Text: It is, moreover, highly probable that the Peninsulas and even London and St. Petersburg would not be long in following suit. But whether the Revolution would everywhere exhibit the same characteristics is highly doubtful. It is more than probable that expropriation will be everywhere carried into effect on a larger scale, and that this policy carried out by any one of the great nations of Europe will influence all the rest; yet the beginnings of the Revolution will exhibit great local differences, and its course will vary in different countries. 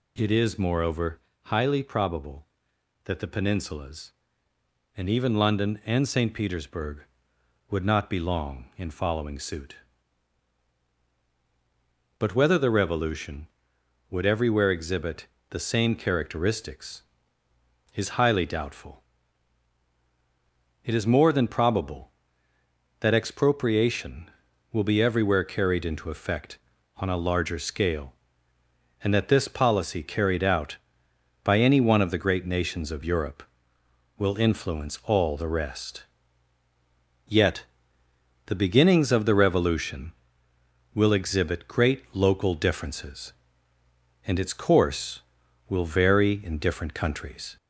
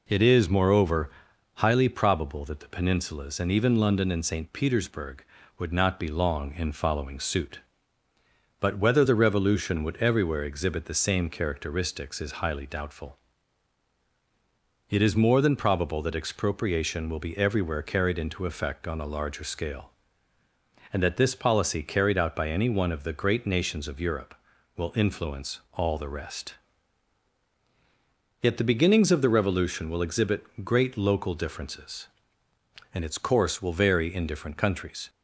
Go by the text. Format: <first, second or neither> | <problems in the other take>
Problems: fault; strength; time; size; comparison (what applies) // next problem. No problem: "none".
second | gets louder; slight; throughout; 3 dB // pauses between "exhibit" and "the"; slight; at 15.2 s; 0.24 s long // pauses between "yet" and "the"; noticeable; at 37.6 s; 0.82 s long